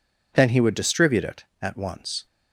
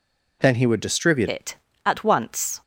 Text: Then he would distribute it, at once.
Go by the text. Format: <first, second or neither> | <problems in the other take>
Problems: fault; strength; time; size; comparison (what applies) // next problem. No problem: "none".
first | changes voice at "it"; from 1.2 s on; 1.4 s long